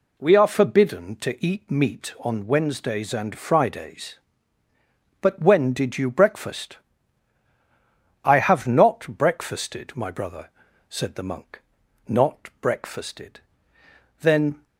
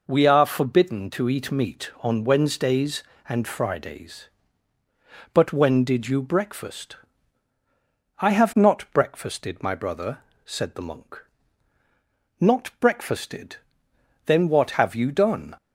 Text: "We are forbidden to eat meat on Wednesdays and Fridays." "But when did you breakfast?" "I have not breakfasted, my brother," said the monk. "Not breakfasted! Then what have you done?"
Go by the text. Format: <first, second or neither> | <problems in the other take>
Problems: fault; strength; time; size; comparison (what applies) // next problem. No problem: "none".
second | stops before "what have you done"; at 14.6 s